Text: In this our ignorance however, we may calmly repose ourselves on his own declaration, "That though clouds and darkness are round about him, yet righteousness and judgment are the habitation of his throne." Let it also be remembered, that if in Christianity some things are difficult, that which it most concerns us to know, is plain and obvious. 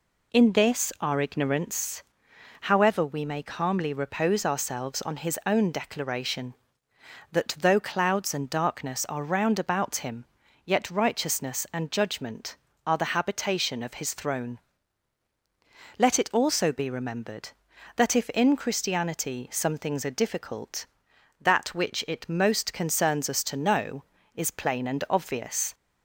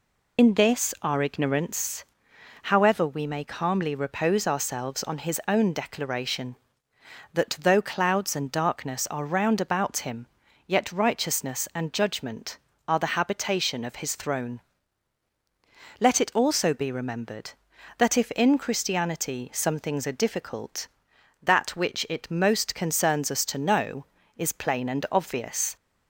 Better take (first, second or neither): first